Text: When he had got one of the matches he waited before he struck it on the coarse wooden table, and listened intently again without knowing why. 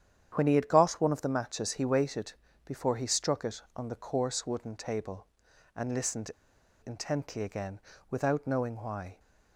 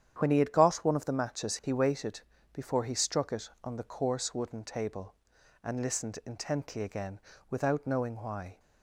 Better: second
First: starts louder than the rest; strong; until 1.3 s; 9.5 dB // pauses between "waited" and "before"; slight; at 2.3 s; 0.32 s long // pauses between "listened" and "intently"; noticeable; at 6.3 s; 0.56 s long // pauses between "again" and "without"; slight; at 7.7 s; 0.30 s long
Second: starts louder than the rest; strong; until 1.1 s; 9 dB // pauses between "waited" and "before"; slight; at 2.2 s; 0.32 s long // pauses between "again" and "without"; slight; at 7.1 s; 0.30 s long

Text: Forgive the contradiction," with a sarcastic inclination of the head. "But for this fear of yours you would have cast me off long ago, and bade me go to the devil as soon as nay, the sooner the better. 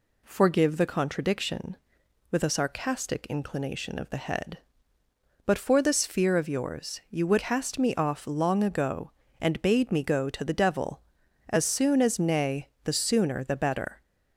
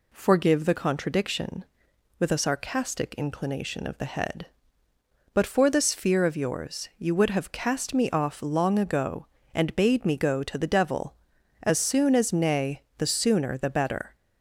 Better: second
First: skips "have"; at 7.3 s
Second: none

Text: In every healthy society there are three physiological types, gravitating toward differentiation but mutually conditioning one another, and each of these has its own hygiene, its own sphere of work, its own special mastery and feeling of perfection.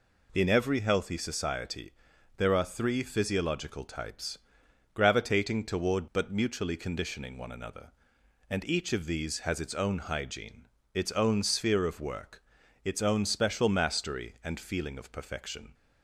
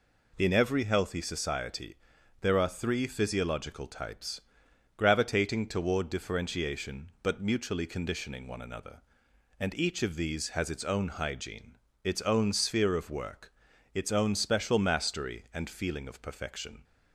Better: second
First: pauses between "society" and "there"; noticeable; at 1.9 s; 0.46 s long // skips "differentiation"; at 6.0 s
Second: pauses between "society" and "there"; noticeable; at 1.9 s; 0.46 s long

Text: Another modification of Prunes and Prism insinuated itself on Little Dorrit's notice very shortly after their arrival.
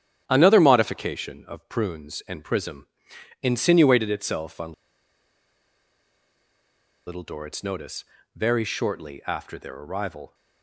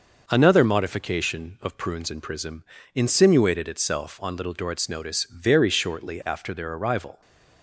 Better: second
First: starts louder than the rest; strong; until 1.2 s; 9.5 dB // pauses between "Prism" and "insinuated"; noticeable; at 2.8 s; 0.56 s long // pauses between "on" and "Little"; strong; at 4.7 s; 2.3 s long // pauses between "notice" and "very"; slight; at 8.0 s; 0.30 s long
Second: pauses between "Prism" and "insinuated"; slight; at 2.6 s; 0.32 s long

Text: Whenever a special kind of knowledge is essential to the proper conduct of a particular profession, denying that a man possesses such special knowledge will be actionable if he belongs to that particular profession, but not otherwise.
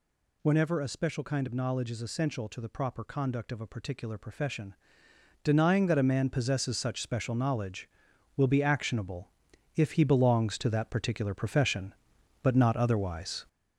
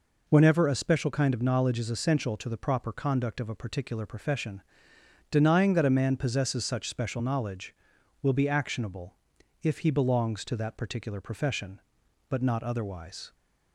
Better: second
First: gets louder; noticeable; throughout; 5.5 dB // pauses between "actionable" and "if"; at 9.3 s; 0.45 s long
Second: pauses between "actionable" and "if"; noticeable; at 9.1 s; 0.46 s long

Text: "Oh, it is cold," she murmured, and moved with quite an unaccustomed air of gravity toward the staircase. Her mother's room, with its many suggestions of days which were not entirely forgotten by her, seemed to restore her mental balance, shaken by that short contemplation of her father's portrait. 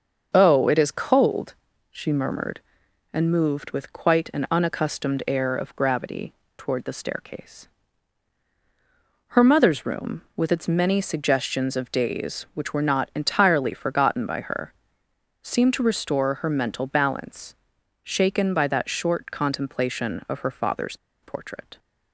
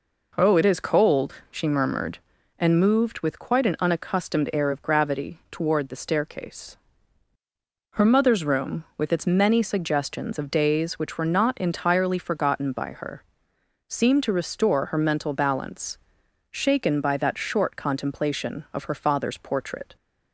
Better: second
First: starts louder than the rest; until 1.3 s; 6.5 dB // pauses between "gravity" and "toward"; slight; at 6.3 s; 0.22 s long // pauses between "father's" and "portrait"; slight; at 20.9 s; 0.26 s long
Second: none

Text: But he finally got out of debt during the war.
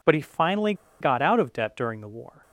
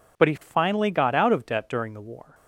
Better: second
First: pauses between "finally" and "got"; slight; at 0.7 s; 0.27 s long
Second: none

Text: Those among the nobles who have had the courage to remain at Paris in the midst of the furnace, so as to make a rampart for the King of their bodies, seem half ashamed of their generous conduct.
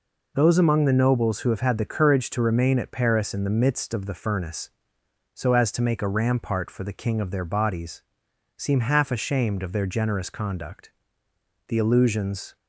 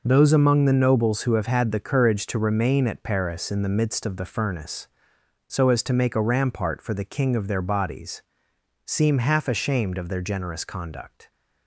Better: second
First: goes on to say "The illusions"; noticeable; from 11.6 s on; 0.88 s long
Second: none

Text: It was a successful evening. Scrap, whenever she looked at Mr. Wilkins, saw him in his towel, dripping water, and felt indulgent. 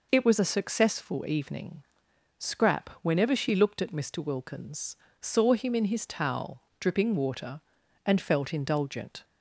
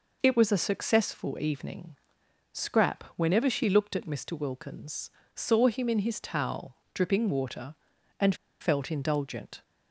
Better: first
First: none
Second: pauses between "and" and "felt"; slight; at 8.3 s; 0.26 s long

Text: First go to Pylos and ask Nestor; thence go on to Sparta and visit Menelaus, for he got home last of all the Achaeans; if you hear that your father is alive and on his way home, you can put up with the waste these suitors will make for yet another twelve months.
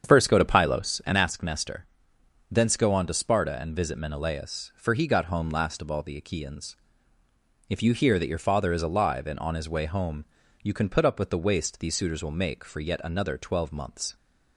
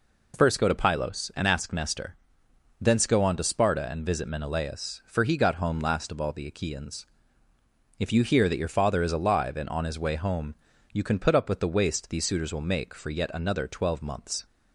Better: second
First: starts louder than the rest; strong; until 1.3 s; 8 dB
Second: none

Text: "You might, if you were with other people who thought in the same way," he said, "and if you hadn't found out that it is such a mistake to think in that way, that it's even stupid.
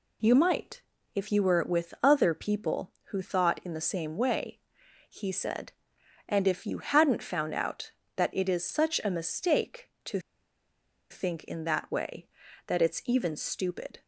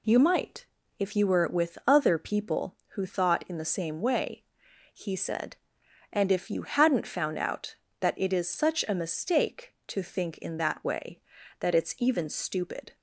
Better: second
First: pauses between "to" and "think"; noticeable; at 10.1 s; 0.91 s long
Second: none

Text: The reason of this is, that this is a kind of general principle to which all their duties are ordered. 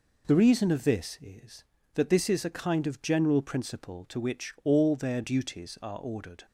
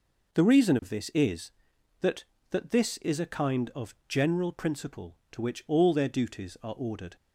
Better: first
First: none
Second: says "that" twice; at 2.4 s

